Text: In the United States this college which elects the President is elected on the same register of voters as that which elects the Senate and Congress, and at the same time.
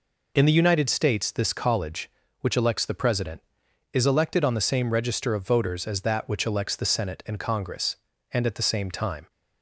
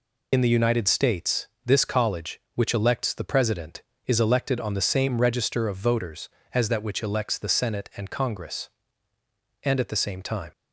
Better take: first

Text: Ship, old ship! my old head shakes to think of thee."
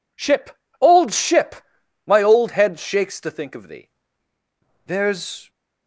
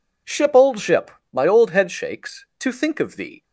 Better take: second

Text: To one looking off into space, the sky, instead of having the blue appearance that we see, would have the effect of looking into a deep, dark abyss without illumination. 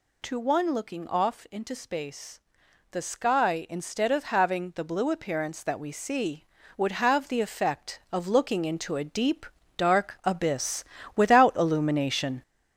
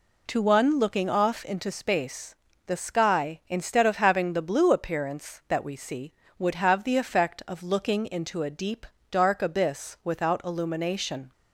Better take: second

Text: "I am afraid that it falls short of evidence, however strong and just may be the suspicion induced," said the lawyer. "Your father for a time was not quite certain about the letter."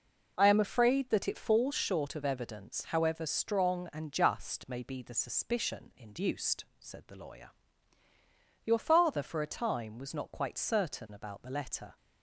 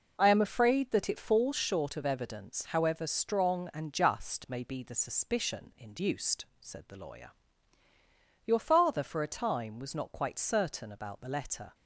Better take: neither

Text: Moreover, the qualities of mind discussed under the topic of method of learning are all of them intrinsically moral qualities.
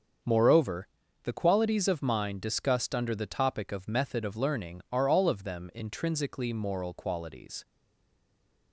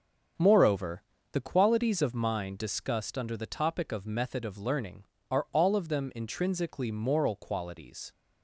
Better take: second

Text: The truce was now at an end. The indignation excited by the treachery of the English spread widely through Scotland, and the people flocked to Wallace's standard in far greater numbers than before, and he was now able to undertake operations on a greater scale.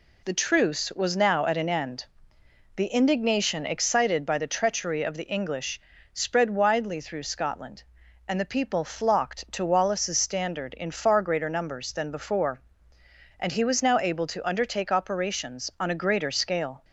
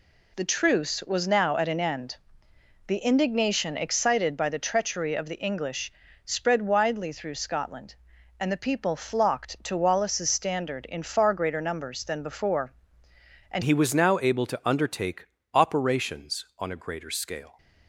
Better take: first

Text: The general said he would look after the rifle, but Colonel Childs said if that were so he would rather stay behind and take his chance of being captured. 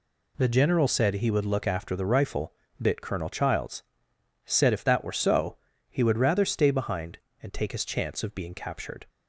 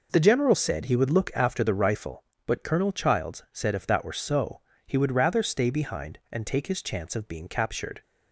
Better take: second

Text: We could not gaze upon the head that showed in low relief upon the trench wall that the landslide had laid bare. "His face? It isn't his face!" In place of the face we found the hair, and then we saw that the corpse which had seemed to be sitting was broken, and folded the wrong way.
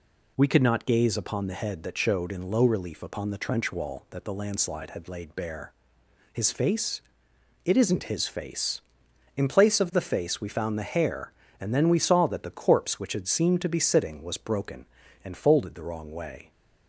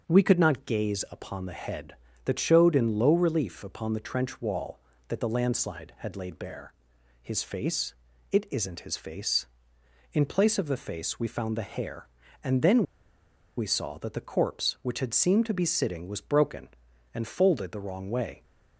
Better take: first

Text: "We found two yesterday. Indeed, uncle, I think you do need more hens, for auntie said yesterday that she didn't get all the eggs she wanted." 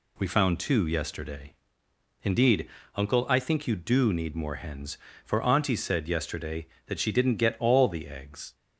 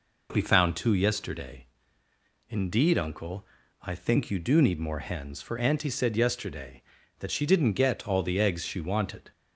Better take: second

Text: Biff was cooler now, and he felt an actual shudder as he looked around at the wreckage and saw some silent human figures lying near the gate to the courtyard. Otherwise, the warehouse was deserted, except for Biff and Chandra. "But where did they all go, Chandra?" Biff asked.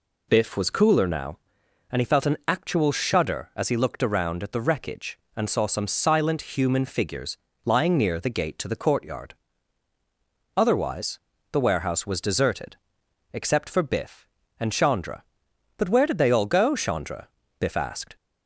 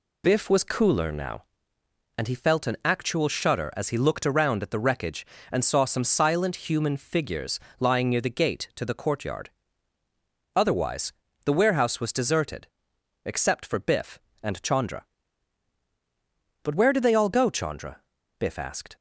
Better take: neither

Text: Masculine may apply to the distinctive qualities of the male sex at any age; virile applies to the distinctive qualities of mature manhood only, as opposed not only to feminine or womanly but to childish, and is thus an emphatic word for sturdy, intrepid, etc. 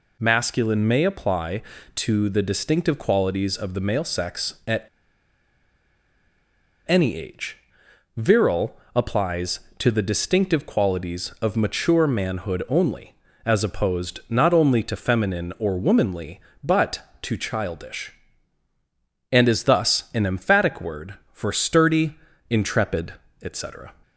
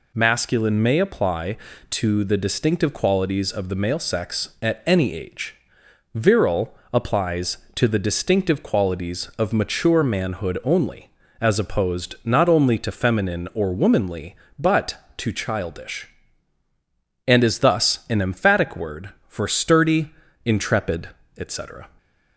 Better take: second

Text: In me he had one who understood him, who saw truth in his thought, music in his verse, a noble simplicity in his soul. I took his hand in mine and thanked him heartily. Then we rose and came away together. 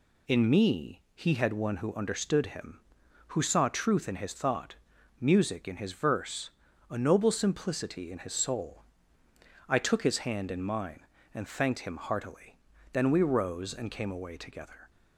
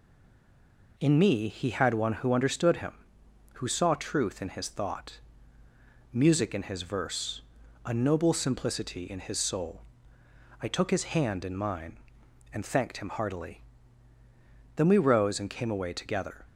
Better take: first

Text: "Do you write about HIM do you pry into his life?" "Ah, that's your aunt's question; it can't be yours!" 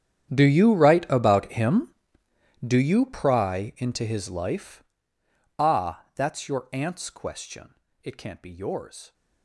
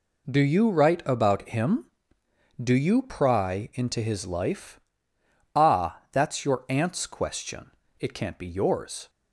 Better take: second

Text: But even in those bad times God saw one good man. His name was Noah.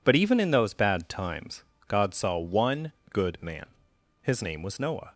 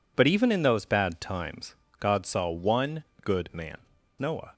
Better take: first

